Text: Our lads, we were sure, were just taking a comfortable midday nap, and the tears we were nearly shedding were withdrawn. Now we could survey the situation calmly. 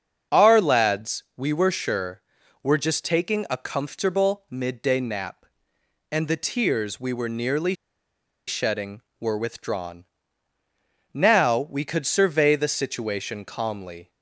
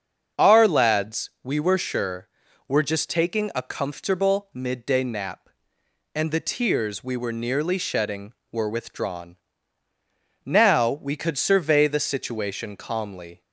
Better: second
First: starts louder than the rest; until 1.4 s; 6.5 dB // pauses between "nearly" and "shedding"; noticeable; at 7.7 s; 0.74 s long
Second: starts louder than the rest; until 1.5 s; 6.5 dB

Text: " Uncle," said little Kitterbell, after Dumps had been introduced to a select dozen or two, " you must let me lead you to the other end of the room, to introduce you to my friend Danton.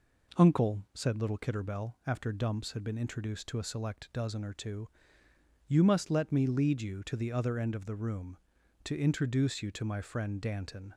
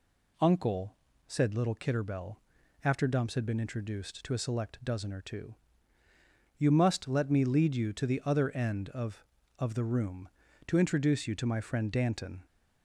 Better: first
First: none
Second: says "of" twice; at 9.5 s

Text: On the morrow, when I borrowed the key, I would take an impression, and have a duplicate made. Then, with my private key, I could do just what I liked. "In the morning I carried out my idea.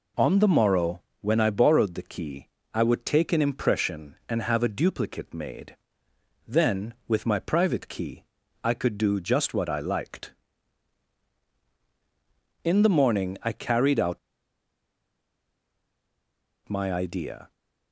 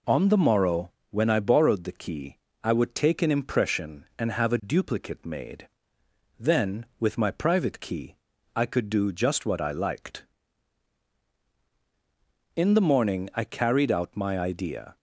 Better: second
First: pauses between "out" and "my"; strong; at 14.1 s; 2.4 s long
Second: none

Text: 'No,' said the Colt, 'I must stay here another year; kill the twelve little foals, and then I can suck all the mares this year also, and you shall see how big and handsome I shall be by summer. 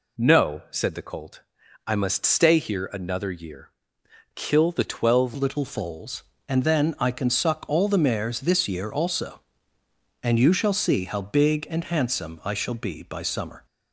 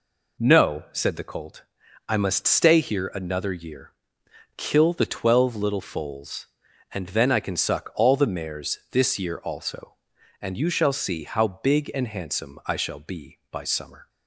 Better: second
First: changes voice at "little"; from 5.3 s on; 8.3 s long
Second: none

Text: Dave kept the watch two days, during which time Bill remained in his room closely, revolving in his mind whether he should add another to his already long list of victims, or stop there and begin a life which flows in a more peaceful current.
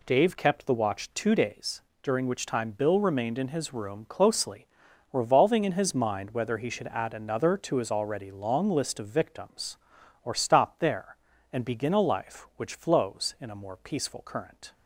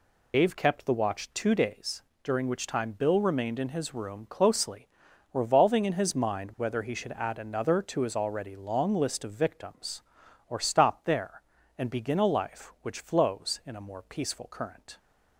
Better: first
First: none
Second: loses the start of "Dave"; at 0.3 s; 135 ms

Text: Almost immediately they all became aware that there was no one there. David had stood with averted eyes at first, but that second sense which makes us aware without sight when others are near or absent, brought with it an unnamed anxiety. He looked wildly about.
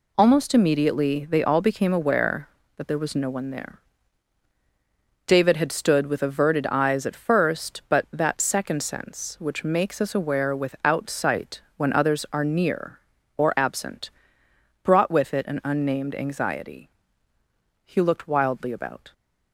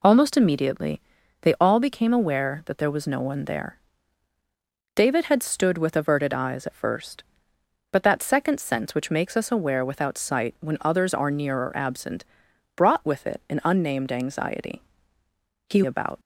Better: first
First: none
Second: pauses between "immediately" and "they"; at 0.9 s; 0.42 s long // skips "looked wildly"; at 15.8 s

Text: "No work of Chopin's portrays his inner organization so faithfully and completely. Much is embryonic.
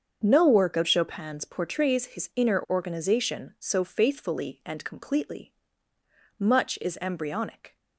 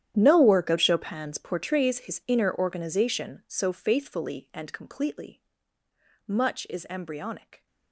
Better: first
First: starts louder than the rest; until 1.2 s; 7 dB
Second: gets quieter; strong; throughout; 18.5 dB // starts louder than the rest; strong; until 1.1 s; 10.5 dB

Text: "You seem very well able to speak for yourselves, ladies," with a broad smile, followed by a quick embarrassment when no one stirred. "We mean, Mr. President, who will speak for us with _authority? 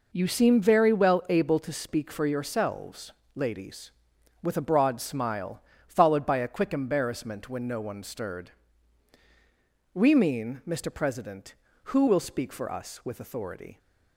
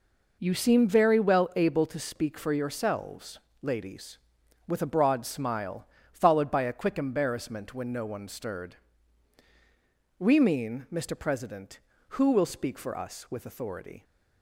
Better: neither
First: none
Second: none

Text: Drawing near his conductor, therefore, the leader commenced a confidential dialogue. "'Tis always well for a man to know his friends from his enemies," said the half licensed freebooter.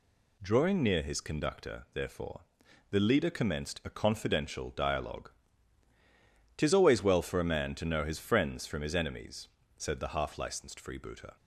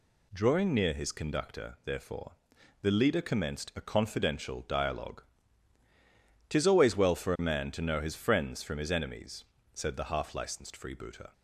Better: neither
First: none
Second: none

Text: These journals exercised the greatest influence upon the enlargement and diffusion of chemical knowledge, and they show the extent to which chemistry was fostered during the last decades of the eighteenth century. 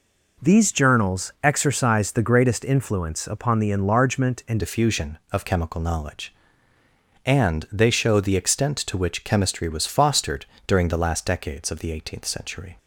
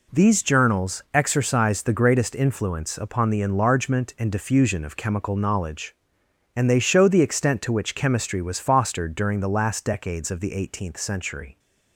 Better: second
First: changes voice at "diffusion"; from 4.5 s on; 8.2 s long // pauses between "fostered" and "during"; slight; at 10.4 s; 0.20 s long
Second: none

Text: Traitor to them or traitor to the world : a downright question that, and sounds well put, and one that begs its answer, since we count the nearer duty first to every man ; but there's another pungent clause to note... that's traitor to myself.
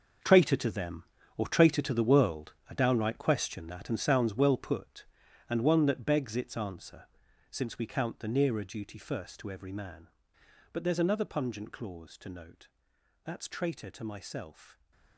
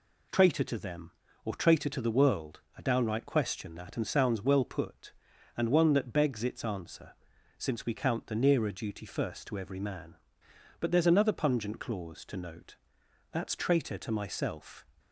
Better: second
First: gets quieter; strong; throughout; 12.5 dB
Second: none

